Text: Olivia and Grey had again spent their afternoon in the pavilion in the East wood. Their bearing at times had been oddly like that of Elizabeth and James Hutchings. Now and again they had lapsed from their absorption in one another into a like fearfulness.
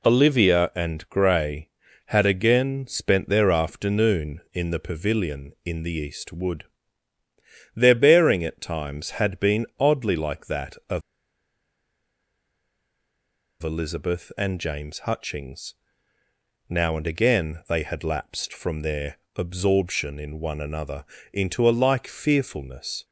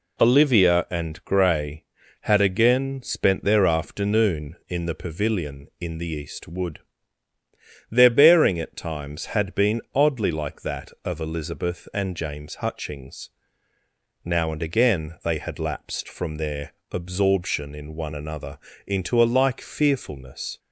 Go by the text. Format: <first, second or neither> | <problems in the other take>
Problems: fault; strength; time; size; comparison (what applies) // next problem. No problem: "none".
second | pauses between "of" and "Elizabeth"; strong; at 11.0 s; 2.6 s long // pauses between "their" and "absorption"; slight; at 19.1 s; 0.18 s long; slight in the second // pauses between "another" and "into"; slight; at 21.0 s; 0.26 s long; slight in the second